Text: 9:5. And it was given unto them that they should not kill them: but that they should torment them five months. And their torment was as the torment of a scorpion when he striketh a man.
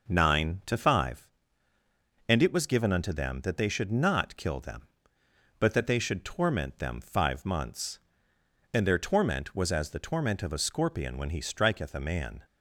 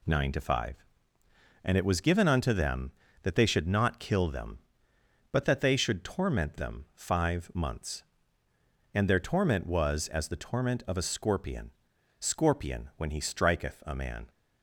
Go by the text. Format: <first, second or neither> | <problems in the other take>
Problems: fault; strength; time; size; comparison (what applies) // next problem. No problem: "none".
first | says "scorpion" twice; at 12.1 s